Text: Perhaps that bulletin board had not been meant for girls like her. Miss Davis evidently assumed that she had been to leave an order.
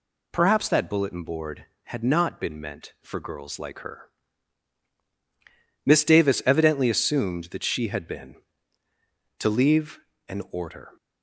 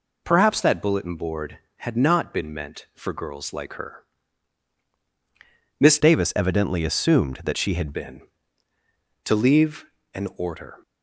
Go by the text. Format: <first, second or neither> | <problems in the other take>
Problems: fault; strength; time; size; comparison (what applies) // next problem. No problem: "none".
first | changes voice from "Davis" to "had"; from 6.0 to 7.9 s; 1.9 s long // pauses between "leave" and "an"; slight; at 9.8 s; 0.28 s long; slight in the first